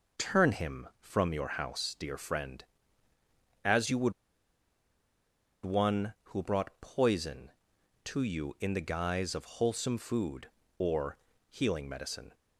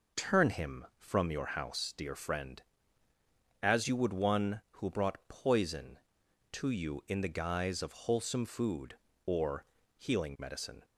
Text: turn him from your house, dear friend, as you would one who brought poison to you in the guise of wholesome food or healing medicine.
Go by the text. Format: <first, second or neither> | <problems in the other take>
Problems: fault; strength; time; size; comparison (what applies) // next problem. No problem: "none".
second | pauses between "would" and "one"; strong; at 4.1 s; 1.5 s long // pauses between "or" and "healing"; slight; at 11.1 s; 0.32 s long; slight in the second